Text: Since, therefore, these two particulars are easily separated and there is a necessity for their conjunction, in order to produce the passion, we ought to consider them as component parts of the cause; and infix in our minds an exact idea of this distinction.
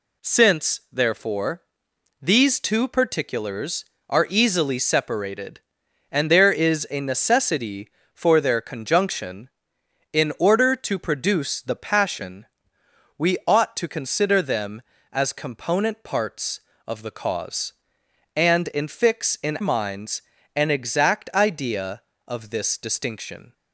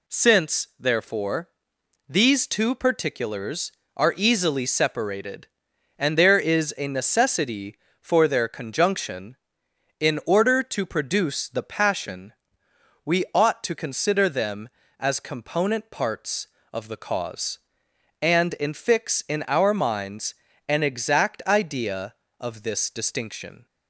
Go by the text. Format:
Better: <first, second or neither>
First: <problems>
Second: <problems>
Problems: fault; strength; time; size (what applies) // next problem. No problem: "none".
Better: second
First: skips "our"; at 19.5 s // pauses between "minds" and "an"; slight; at 20.2 s; 0.34 s long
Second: pauses between "minds" and "an"; slight; at 20.3 s; 0.34 s long